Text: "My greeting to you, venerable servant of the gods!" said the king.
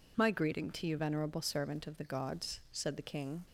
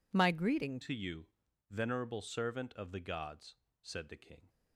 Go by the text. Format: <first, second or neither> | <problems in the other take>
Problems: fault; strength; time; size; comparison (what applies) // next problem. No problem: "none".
first | changes voice at "to"; from 0.8 s on; 3.6 s long